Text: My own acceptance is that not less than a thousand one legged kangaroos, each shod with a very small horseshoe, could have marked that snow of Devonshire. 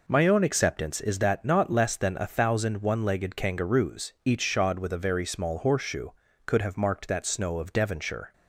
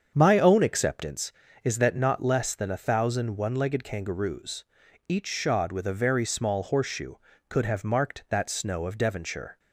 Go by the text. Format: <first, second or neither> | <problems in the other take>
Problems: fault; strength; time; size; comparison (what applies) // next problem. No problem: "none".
first | starts louder than the rest; strong; until 1.0 s; 7.5 dB